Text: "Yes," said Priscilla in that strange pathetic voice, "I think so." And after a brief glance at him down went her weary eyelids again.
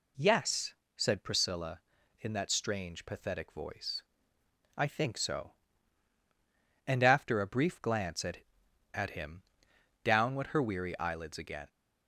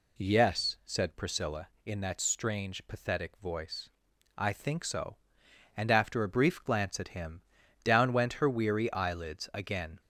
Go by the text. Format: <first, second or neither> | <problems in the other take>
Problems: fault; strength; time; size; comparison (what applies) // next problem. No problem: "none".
second | says "at" twice; at 8.9 s // pauses between "him" and "down"; noticeable; at 9.4 s; 0.62 s long; also in the second